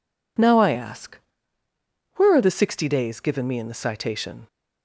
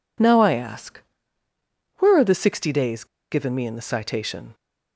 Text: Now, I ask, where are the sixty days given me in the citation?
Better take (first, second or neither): first